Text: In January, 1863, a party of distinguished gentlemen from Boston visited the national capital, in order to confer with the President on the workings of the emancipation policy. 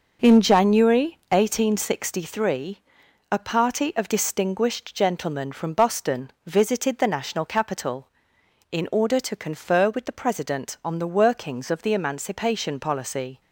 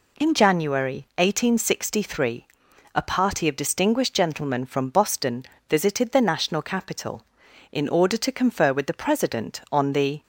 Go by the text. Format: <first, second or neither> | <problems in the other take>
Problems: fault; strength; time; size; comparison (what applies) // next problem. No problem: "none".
first | pauses between "Boston" and "visited"; slight; at 5.4 s; 0.24 s long // stops before "workings of the emancipation policy"; at 10.2 s